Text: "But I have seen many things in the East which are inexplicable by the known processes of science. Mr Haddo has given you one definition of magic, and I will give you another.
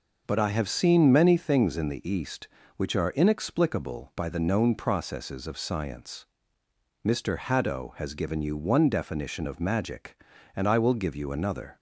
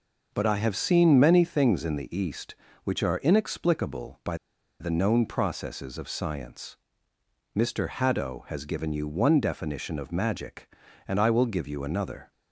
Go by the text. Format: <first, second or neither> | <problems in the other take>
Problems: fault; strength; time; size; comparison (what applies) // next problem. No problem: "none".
first | pauses between "by" and "the"; at 4.3 s; 0.43 s long